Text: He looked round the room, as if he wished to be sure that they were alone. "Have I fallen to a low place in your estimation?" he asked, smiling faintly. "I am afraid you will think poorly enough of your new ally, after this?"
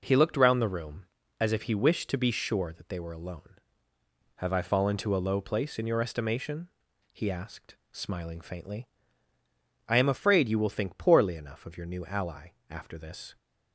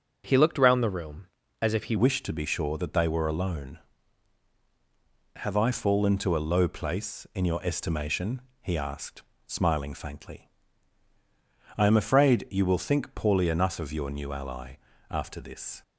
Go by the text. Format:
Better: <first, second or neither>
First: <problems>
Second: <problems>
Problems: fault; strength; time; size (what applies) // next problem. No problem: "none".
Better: first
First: none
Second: starts louder than the rest; until 1.2 s; 6.5 dB // changes voice at "wished"; from 1.9 s on; 13.9 s long